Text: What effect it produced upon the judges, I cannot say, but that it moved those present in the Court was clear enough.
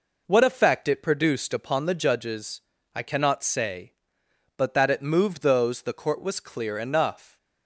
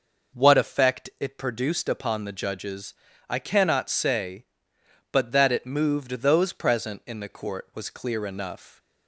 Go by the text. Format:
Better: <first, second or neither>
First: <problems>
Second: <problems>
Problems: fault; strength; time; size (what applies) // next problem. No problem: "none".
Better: second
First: skips "present in"; at 5.8 s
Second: none